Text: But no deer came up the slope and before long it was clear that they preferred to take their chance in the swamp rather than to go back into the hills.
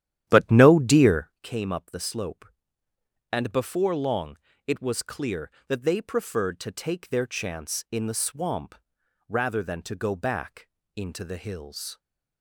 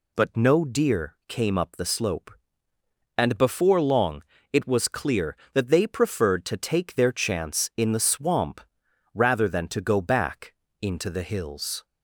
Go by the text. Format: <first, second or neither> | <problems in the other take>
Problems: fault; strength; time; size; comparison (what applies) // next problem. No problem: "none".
second | starts louder than the rest; strong; until 1.4 s; 11.5 dB // pauses between "long" and "it"; slight; at 4.3 s; 0.28 s long; slight in the second // pauses between "swamp" and "rather"; noticeable; at 8.7 s; 0.54 s long; noticeable in the second // pauses between "back" and "into"; slight; at 10.6 s; 0.26 s long; slight in the second